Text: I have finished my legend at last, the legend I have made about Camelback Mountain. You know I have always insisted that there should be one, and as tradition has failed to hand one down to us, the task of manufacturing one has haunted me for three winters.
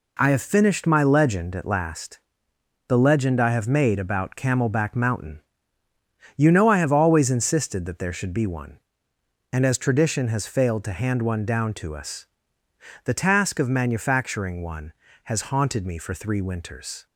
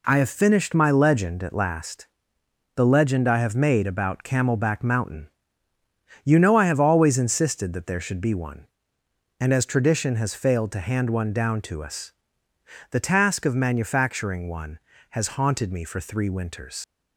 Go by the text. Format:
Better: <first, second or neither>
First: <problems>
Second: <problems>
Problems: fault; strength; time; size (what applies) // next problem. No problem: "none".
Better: first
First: none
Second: leaves "winters" unfinished; at 16.8 s; 95 ms